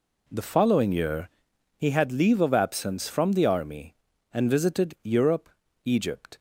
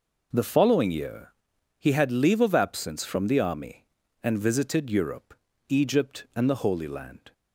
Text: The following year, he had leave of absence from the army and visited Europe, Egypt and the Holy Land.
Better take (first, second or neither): second